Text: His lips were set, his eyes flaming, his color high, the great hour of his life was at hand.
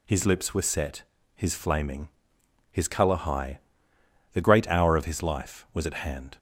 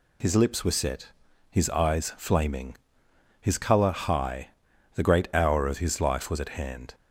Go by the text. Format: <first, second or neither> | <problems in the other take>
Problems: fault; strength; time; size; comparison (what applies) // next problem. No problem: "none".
second | skips "eyes"; at 1.5 s